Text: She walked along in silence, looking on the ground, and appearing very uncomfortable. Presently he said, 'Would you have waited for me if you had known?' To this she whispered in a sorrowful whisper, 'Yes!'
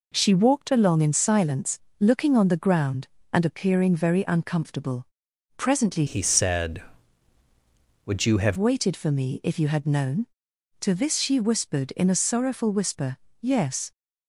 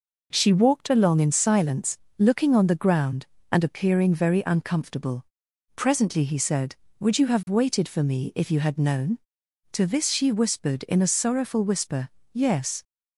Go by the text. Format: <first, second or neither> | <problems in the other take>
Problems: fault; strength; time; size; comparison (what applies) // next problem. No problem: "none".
second | changes voice from "he" to "have"; from 6.0 to 8.5 s; 2.5 s long